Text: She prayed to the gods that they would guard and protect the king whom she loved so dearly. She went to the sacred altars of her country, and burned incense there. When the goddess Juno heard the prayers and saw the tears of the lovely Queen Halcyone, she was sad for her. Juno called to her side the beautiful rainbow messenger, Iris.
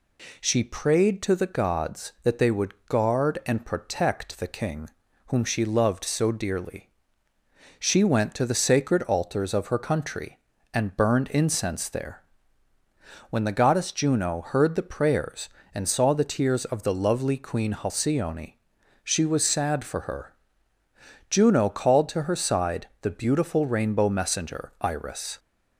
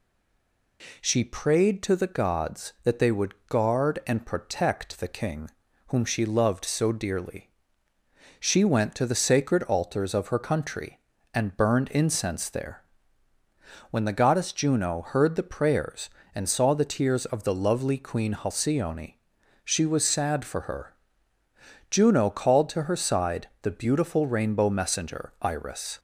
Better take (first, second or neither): first